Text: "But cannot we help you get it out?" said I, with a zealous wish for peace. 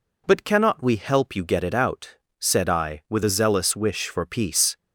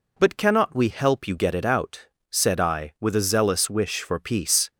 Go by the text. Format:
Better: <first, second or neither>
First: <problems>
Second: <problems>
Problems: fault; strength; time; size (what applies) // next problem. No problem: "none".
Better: neither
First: none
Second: none